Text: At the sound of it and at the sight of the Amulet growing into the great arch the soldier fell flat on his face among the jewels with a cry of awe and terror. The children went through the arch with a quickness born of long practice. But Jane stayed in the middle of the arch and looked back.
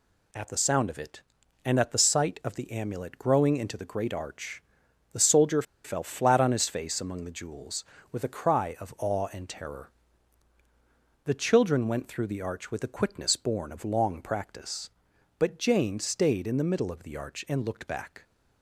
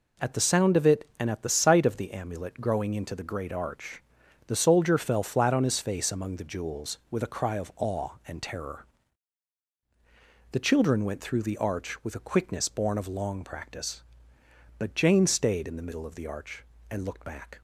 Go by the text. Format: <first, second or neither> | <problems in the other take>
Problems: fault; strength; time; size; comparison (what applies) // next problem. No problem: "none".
second | pauses between "arch" and "the"; noticeable; at 4.6 s; 0.50 s long; noticeable in the second // pauses between "soldier" and "fell"; slight; at 5.6 s; 0.22 s long